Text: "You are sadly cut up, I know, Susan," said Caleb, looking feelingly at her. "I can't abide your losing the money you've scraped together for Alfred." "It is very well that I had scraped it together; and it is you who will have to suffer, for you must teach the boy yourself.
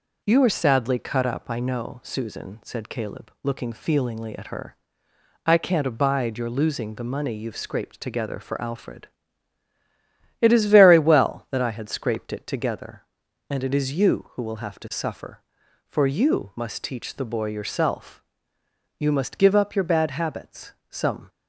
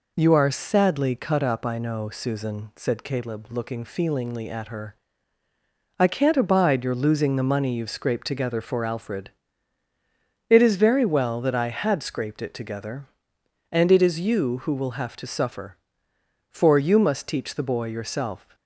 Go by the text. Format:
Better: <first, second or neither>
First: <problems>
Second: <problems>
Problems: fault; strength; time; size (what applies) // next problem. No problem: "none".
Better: second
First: goes on to say "You must give up your bad habits Some"; strong; from 18.9 s on; 2.3 s long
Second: none